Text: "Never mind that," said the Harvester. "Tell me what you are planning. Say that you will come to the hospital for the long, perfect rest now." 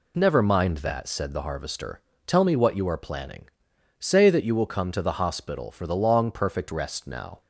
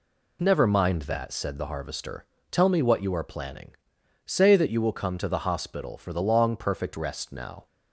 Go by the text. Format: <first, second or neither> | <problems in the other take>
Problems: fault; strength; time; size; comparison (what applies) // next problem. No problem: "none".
neither | none